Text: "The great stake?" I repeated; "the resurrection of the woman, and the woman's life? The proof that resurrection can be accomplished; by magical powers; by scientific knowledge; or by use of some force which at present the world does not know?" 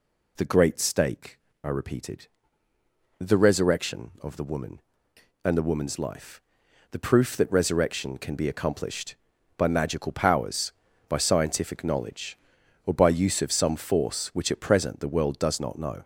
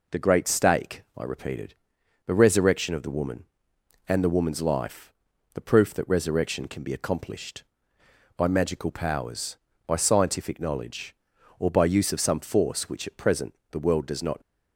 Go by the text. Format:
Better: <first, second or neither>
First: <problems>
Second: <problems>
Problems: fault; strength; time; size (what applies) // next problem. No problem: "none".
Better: first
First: none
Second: pauses between "present" and "the"; slight; at 13.5 s; 0.16 s long // stops before "know"; at 14.3 s